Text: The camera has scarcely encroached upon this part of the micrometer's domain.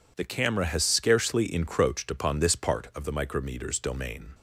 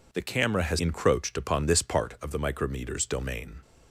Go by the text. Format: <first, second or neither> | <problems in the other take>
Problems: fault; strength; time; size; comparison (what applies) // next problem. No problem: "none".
first | skips "scarcely"; at 0.8 s